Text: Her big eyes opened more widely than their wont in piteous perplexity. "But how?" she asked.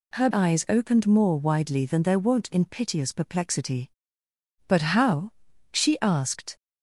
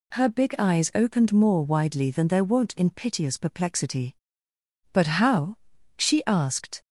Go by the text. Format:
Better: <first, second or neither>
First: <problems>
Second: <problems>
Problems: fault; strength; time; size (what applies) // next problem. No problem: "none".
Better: second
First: skips "big"; at 0.2 s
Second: none